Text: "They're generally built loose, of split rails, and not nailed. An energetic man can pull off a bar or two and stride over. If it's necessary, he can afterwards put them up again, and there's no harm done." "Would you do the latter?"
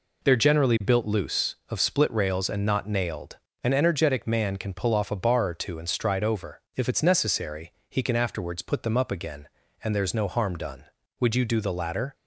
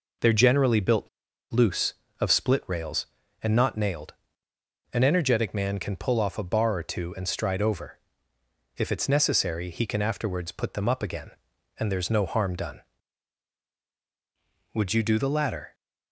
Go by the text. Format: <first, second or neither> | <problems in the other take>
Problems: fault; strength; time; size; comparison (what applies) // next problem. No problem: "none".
first | pauses between "built" and "loose"; at 1.0 s; 0.43 s long